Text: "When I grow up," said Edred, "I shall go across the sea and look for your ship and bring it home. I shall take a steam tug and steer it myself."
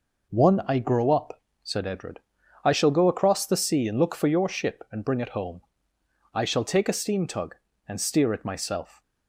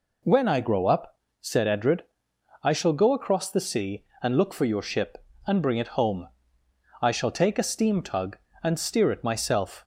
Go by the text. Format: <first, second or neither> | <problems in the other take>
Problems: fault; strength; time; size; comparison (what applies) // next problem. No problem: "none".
second | says "One" for "When"; at 0.2 s